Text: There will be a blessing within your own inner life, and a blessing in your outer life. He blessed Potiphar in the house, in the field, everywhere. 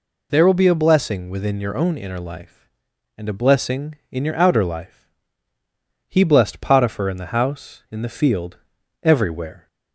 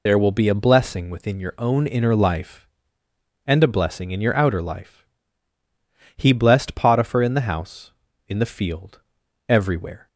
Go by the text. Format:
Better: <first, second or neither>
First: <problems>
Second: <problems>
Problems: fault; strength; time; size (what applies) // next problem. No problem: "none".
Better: first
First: none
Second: loses the start of "There"; at 0.0 s; 40 ms